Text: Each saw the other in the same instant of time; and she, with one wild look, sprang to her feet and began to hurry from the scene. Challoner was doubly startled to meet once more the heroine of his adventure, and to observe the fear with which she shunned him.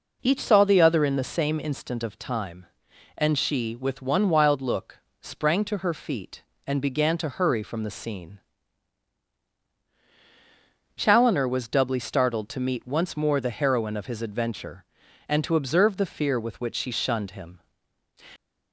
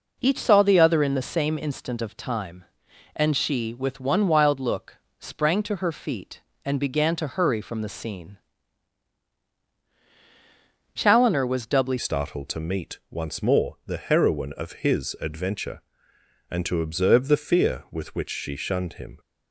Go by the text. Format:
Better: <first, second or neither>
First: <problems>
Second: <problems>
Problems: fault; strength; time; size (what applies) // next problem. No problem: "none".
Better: first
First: none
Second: changes voice at "startled"; from 11.9 s on; 7.2 s long